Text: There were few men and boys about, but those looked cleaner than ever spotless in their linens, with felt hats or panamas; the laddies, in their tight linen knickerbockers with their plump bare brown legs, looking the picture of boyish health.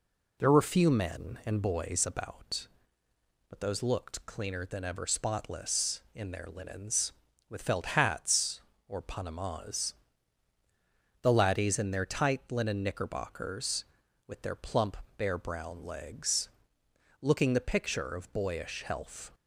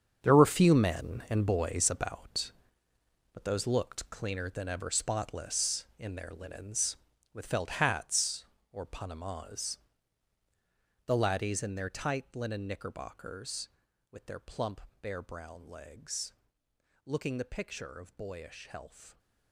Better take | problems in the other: first | gets quieter; strong; throughout; 12.5 dB // pauses between "plump" and "bare"; slight; at 14.8 s; 0.20 s long; slight in the first

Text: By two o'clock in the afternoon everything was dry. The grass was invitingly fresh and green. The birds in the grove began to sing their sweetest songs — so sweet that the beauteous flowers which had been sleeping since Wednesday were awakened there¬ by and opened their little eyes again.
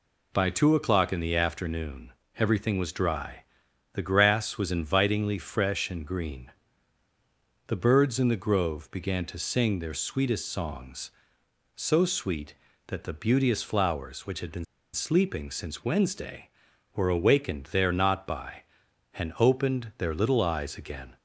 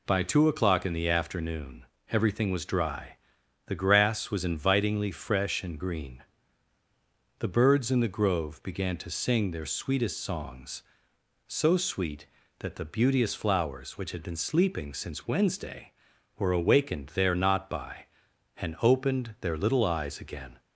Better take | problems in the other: second | pauses between "afternoon" and "everything"; slight; at 2.1 s; 0.26 s long; slight in the second // pauses between "been" and "sleeping"; slight; at 14.6 s; 0.29 s long

